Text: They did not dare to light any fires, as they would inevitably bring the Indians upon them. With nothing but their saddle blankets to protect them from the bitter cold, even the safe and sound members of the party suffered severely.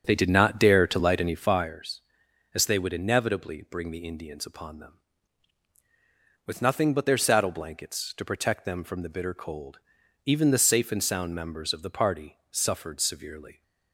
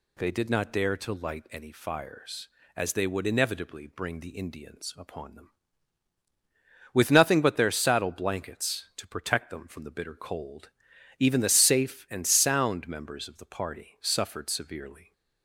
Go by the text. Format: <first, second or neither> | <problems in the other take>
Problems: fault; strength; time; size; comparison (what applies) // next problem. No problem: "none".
second | starts louder than the rest; strong; until 1.8 s; 7.5 dB